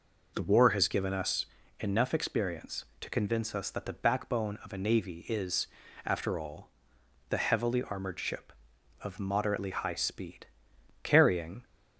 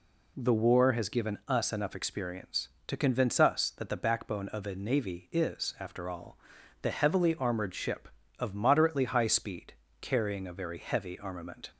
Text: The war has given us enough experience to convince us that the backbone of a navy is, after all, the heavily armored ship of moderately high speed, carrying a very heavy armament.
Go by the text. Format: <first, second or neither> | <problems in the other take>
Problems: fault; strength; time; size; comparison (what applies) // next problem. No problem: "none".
second | pauses between "us" and "enough"; slight; at 1.4 s; 0.32 s long // stops before "a very heavy armament"; at 11.6 s